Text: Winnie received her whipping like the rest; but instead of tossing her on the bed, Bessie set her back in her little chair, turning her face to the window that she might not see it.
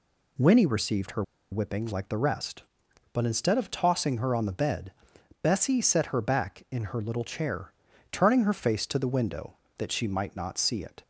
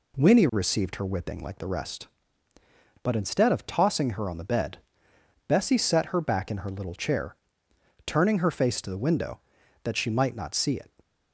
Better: second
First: pauses between "her" and "whipping"; slight; at 1.2 s; 0.28 s long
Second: none

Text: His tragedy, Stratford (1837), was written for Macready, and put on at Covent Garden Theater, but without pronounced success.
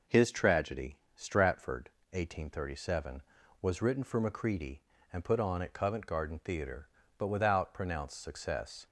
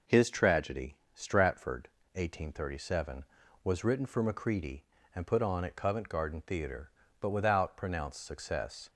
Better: neither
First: none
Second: none

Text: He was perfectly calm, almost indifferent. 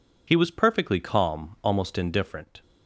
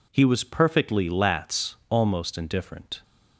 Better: first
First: none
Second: says "lats" for "calm"; at 1.0 s

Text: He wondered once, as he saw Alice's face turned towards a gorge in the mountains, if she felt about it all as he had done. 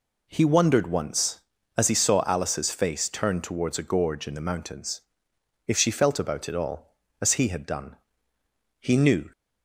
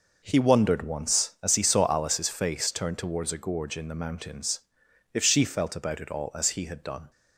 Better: second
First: goes on to say "He knew"; from 8.7 s on; 0.52 s long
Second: none

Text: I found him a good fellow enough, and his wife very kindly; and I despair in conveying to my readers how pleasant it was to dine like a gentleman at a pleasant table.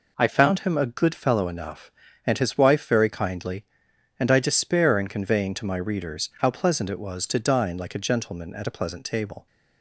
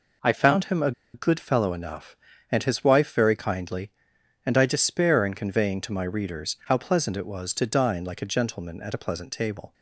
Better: first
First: none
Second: pauses between "a" and "good"; slight; at 0.9 s; 0.22 s long

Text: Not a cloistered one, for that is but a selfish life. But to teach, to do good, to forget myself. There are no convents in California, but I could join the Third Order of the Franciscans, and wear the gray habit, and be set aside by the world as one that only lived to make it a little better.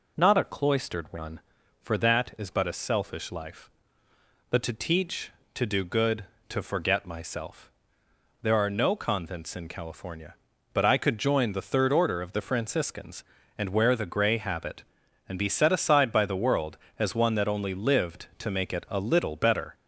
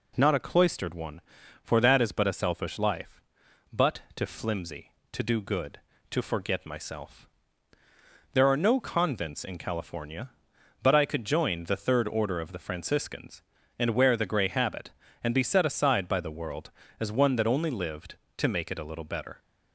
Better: first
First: none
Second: says "flimsy" for "teach"; at 4.2 s

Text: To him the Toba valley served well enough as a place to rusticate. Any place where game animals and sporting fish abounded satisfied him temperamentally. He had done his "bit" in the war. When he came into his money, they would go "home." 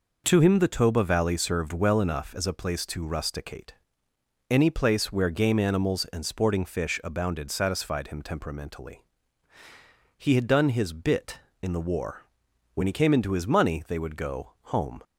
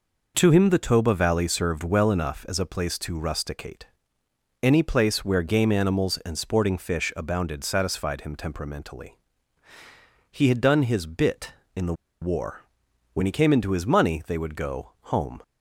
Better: first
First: none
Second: pauses between "the" and "war"; slight; at 11.9 s; 0.27 s long

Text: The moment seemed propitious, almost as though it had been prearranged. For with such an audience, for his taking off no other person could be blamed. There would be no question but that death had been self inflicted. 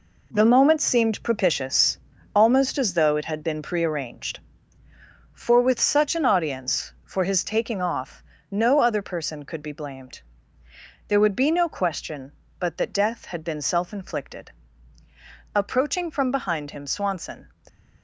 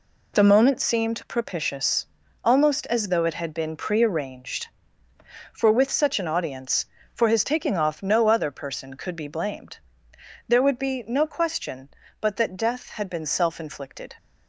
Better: second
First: pauses between "off" and "no"; slight; at 8.2 s; 0.26 s long // goes on to say "Approaching from behind him Swanson"; strong; from 15.5 s on; 1.9 s long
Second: none

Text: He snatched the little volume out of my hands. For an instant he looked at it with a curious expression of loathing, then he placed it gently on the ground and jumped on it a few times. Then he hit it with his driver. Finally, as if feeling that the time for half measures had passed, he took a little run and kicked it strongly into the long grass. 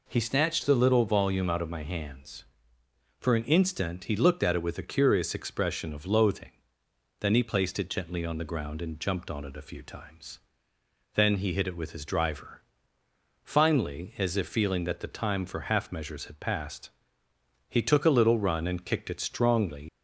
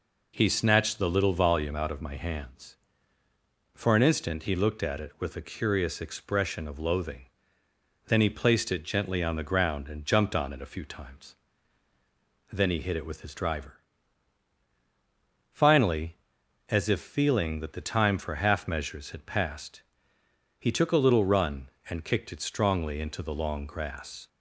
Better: second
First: stops before "into the long grass"; at 19.8 s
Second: none

